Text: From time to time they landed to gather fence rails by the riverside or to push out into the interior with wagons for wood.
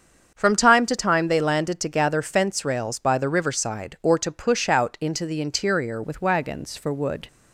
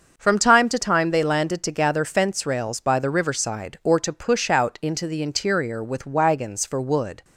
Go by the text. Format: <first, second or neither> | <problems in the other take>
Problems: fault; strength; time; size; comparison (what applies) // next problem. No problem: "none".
second | starts louder than the rest; strong; until 1.3 s; 7.5 dB; also in the second // changes voice at "with"; from 6.0 s on; 1.2 s long